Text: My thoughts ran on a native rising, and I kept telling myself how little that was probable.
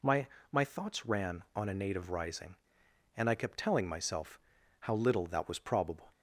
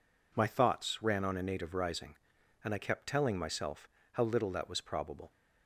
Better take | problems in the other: second | says "My" twice; at 0.5 s // pauses between "myself" and "how"; at 4.3 s; 0.40 s long; slight in the second

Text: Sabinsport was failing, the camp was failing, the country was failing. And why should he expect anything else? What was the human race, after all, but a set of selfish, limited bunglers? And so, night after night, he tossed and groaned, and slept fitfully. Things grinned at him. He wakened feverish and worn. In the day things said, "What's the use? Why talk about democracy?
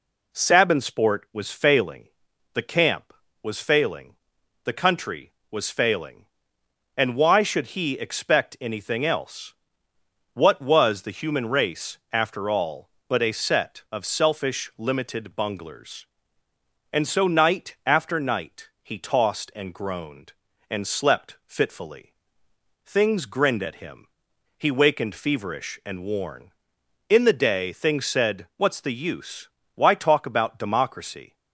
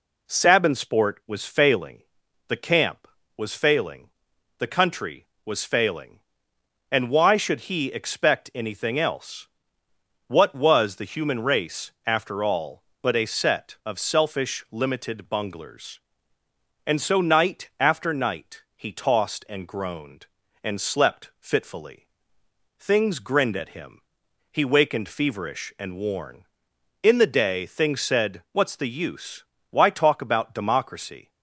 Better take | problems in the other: neither | none

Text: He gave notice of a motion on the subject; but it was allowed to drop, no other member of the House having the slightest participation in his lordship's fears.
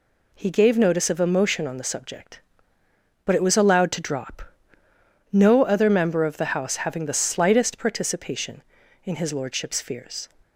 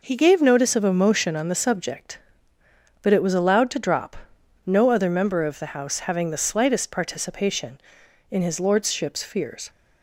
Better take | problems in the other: neither | none

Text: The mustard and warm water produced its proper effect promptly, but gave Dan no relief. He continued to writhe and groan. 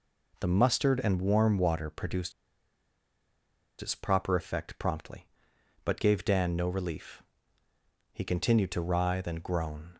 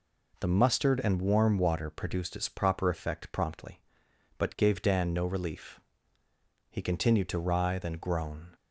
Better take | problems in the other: second | pauses between "produced" and "its"; strong; at 2.3 s; 1.4 s long

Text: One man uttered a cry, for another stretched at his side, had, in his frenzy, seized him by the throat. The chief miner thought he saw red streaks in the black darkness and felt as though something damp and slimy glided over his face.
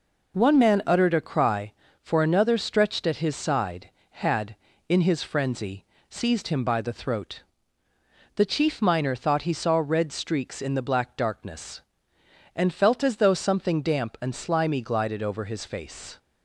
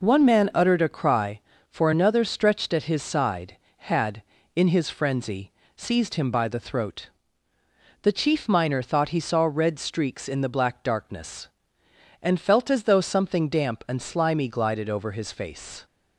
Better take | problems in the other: neither | none

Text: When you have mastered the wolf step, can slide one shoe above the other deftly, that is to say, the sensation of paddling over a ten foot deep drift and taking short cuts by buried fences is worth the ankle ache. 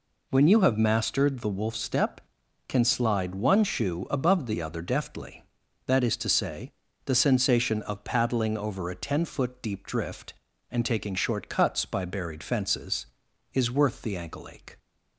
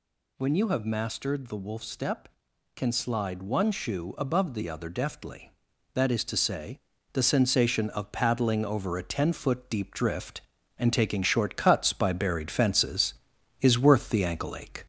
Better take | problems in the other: first | gets louder; slight; throughout; 2.5 dB

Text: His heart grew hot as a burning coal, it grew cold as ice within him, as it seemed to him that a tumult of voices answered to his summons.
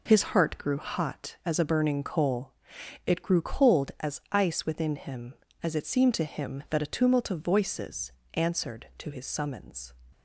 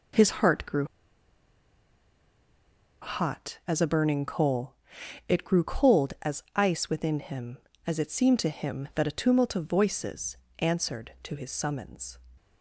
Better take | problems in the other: first | pauses between "grew" and "hot"; strong; at 0.8 s; 2.1 s long // pauses between "voices" and "answered"; slight; at 10.3 s; 0.24 s long; slight in the first

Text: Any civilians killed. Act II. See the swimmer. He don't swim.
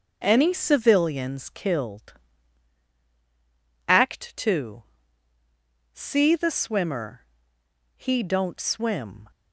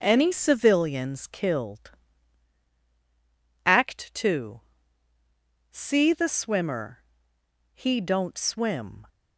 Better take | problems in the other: neither | none

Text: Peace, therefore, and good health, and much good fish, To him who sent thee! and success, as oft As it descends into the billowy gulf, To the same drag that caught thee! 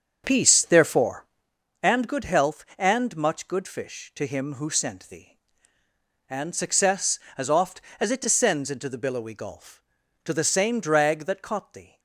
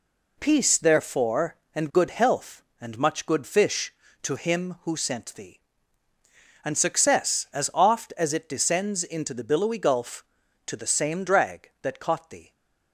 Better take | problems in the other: second | starts louder than the rest; until 1.6 s; 6.5 dB

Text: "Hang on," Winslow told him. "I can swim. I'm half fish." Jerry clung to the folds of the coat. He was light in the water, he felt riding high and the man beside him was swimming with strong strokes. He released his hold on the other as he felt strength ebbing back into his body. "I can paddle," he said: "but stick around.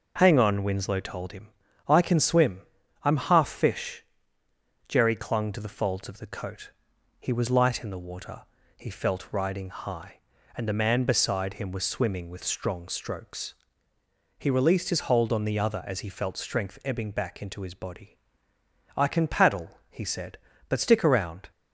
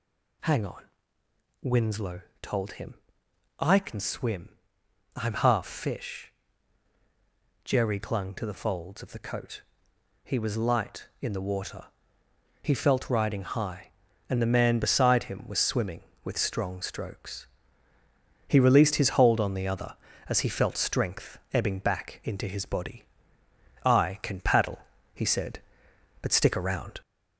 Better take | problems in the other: first | gets louder; noticeable; throughout; 4 dB // pauses between "Winslow" and "told"; slight; at 2.2 s; 0.18 s long // pauses between "strength" and "ebbing"; slight; at 21.3 s; 0.16 s long

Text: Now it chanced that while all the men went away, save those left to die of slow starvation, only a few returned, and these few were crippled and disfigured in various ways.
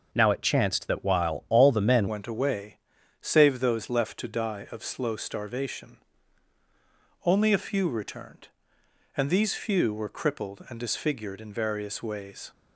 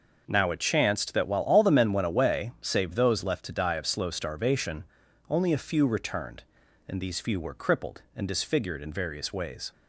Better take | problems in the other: second | changes voice at "went"; from 2.0 s on; 10.5 s long

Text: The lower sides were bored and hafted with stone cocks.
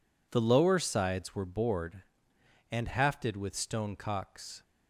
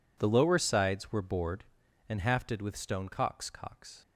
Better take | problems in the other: first | says "cocks" twice; at 3.4 s

